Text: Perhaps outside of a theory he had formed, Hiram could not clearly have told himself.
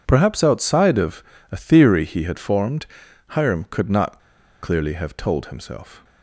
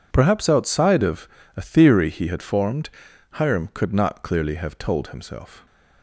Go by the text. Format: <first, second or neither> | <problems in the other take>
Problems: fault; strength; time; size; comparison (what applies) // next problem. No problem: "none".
second | pauses between "of" and "a"; slight; at 1.2 s; 0.26 s long; slight in the second // pauses between "not" and "clearly"; at 4.1 s; 0.42 s long